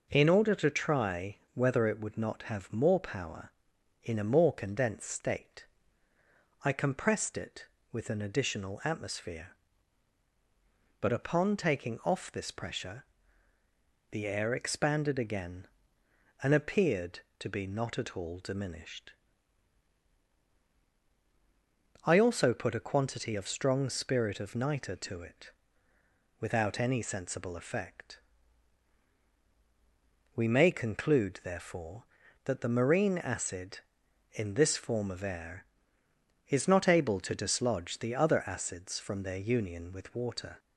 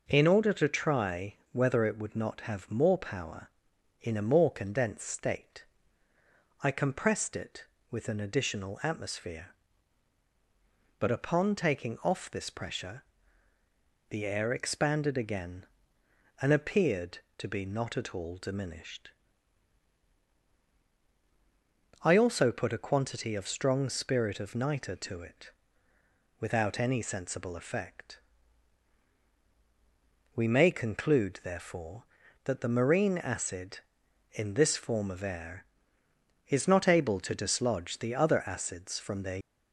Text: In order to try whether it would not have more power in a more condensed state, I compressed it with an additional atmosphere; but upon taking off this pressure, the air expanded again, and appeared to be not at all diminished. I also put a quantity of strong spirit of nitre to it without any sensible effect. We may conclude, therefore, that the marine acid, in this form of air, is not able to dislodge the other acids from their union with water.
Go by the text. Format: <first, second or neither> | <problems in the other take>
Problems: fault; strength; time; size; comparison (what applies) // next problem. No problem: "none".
first | pauses between "try" and "whether"; slight; at 1.3 s; 0.16 s long; slight in the first // pauses between "it" and "without"; noticeable; at 25.5 s; 0.88 s long; noticeable in the first // stops before "union with water"; at 39.4 s